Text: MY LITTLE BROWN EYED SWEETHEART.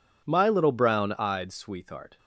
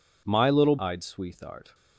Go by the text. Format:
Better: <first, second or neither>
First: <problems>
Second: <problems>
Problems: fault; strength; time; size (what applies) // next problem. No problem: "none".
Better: first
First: none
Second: skips "BROWN"; at 0.7 s